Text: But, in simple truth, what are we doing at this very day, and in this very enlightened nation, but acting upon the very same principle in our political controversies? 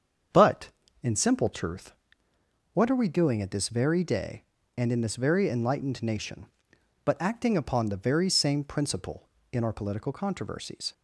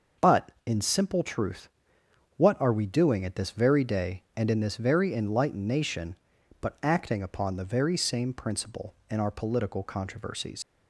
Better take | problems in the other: first | starts louder than the rest; until 1.3 s; 6 dB; strong in the first // leaves "controversies" unfinished; at 10.6 s; 135 ms

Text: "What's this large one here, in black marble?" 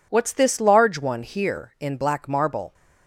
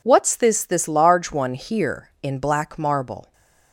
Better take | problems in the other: first | says "this" twice; at 0.6 s

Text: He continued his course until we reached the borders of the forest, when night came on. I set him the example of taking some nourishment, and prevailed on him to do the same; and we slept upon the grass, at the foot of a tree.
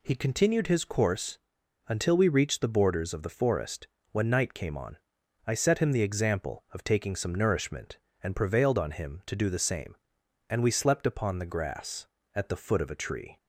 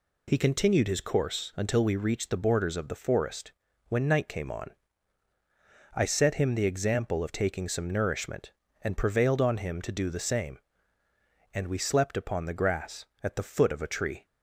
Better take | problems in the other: second | pauses between "course" and "until"; noticeable; at 1.3 s; 0.48 s long

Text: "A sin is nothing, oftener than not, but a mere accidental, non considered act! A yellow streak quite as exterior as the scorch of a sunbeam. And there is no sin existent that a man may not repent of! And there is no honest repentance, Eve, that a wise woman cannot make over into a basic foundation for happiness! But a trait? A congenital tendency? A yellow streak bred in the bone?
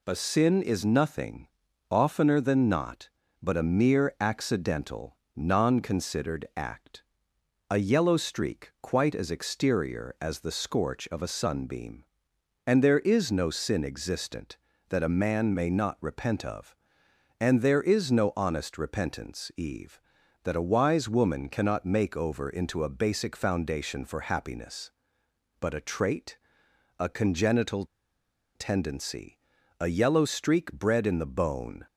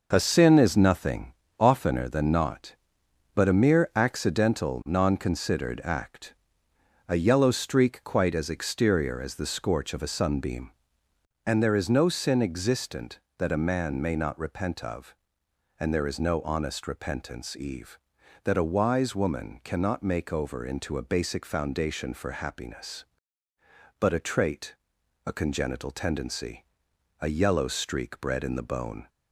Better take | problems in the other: second | pauses between "congenital" and "tendency"; noticeable; at 27.8 s; 0.71 s long

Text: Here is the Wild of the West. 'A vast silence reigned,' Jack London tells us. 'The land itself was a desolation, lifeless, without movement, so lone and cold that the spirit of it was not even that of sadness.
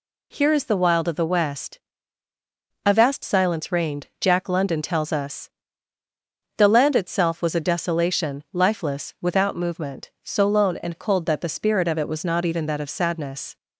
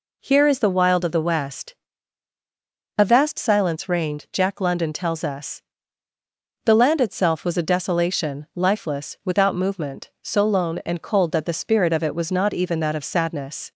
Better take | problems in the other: neither | none

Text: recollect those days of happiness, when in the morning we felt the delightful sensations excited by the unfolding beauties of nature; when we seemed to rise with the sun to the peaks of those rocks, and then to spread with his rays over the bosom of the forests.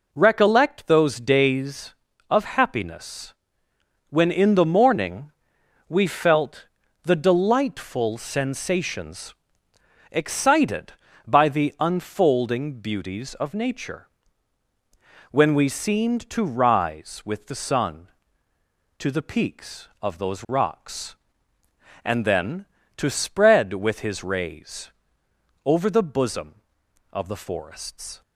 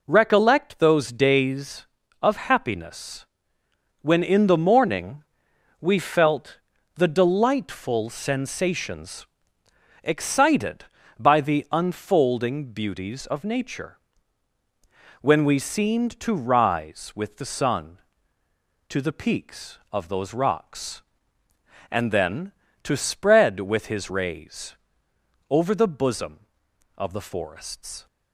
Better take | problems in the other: neither | pauses between "morning" and "we"; noticeable; the same in both // pauses between "felt" and "the"; slight; the same in both // pauses between "sensations" and "excited"; noticeable; the same in both // pauses between "rays" and "over"; noticeable; the same in both

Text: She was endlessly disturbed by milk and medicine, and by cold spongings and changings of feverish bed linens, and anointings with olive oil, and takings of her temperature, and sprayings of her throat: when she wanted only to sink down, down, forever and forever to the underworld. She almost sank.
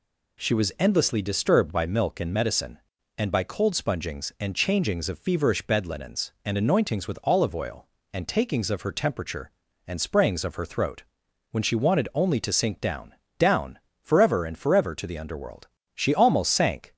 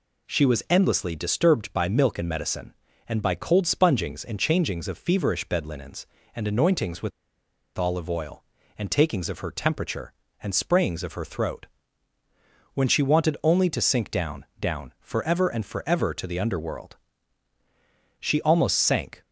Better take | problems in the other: first | pauses between "with" and "olive"; noticeable; at 7.1 s; 0.67 s long

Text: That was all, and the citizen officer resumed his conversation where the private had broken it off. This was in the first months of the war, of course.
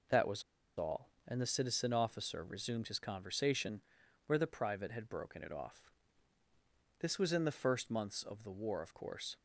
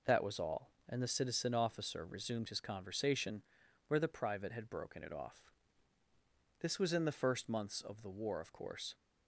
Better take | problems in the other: second | pauses between "was" and "all"; slight; at 0.4 s; 0.35 s long // pauses between "conversation" and "where"; at 3.8 s; 0.44 s long; also in the second

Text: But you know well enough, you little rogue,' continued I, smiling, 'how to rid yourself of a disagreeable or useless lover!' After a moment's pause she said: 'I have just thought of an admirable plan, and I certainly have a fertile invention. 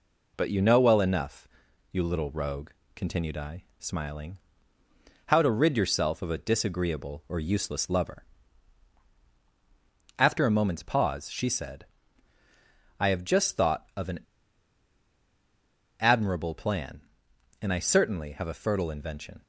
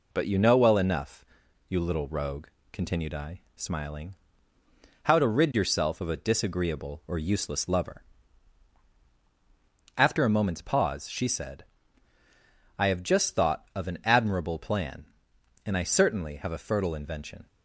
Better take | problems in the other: second | pauses between "an" and "admirable"; strong; at 14.1 s; 1.8 s long

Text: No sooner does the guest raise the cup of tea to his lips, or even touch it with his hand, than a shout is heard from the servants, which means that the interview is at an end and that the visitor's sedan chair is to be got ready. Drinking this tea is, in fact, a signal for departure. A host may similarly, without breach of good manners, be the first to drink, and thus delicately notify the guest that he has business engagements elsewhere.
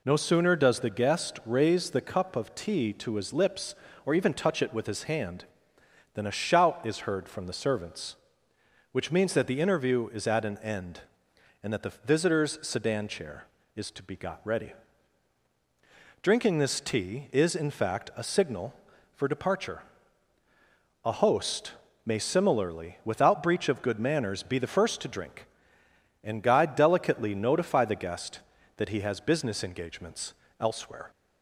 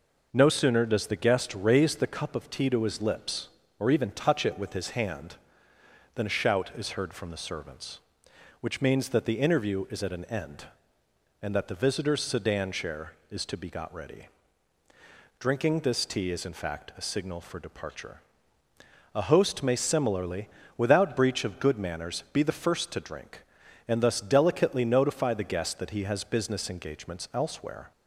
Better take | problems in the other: second | pauses between "host" and "may"; slight; at 21.7 s; 0.34 s long // says "guide" for "thus"; at 26.4 s // pauses between "engagements" and "elsewhere"; slight; at 30.3 s; 0.26 s long

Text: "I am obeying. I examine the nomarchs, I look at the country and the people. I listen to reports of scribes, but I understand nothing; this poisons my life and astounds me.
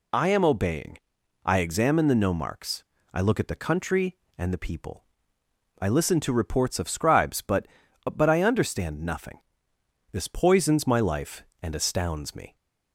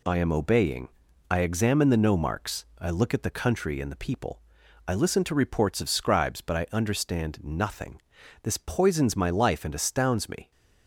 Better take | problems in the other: second | says "but" twice; at 8.0 s

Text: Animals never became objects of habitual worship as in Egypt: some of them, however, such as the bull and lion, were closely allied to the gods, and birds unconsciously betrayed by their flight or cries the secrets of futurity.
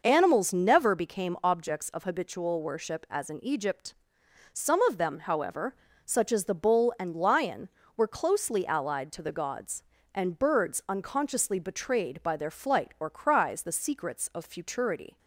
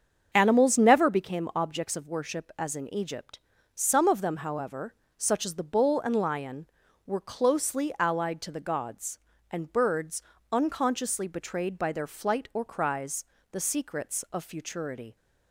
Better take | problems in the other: first | starts louder than the rest; until 1.3 s; 7 dB // skips "habitual"; at 2.0 s // pauses between "birds" and "unconsciously"; slight; at 10.2 s; 0.30 s long // pauses between "cries" and "the"; slight; at 13.2 s; 0.28 s long

